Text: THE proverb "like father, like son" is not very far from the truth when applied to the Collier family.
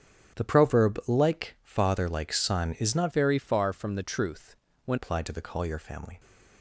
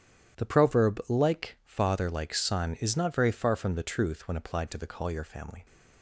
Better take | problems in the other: second | starts louder than the rest; strong; until 1.4 s; 9 dB; strong in the second // changes voice from "very" to "when"; from 3.1 to 4.9 s; 1.8 s long // pauses between "truth" and "when"; slight; at 4.5 s; 0.32 s long

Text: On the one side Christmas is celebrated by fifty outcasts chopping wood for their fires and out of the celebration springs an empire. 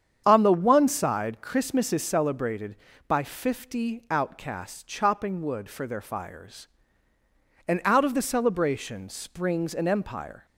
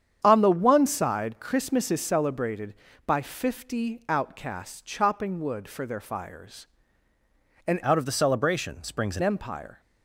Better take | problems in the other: first | starts louder than the rest; strong; until 1.2 s; 8.5 dB; strong in the first // changes voice from "out" to "an"; from 7.8 to 9.2 s; 1.4 s long

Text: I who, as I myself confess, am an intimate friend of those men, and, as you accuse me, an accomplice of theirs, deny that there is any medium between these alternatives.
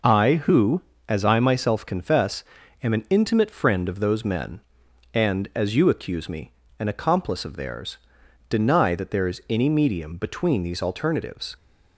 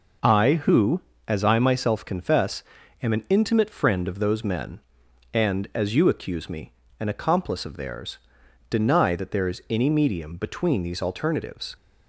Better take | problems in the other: neither | none

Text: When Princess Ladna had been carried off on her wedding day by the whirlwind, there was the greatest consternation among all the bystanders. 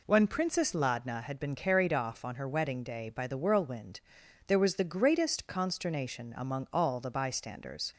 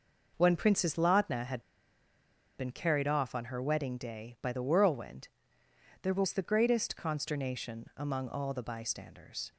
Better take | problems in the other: first | pauses between "had" and "been"; noticeable; at 1.6 s; 0.95 s long

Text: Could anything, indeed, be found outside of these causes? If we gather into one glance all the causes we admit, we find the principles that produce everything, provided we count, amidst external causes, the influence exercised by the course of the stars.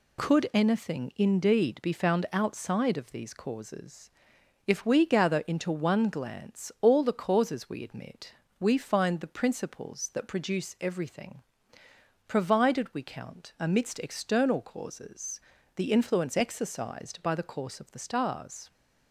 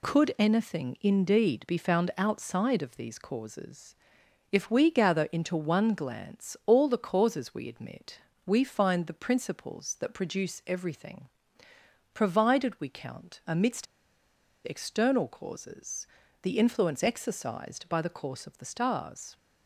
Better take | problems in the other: first | pauses between "amidst" and "external"; noticeable; at 13.8 s; 0.79 s long

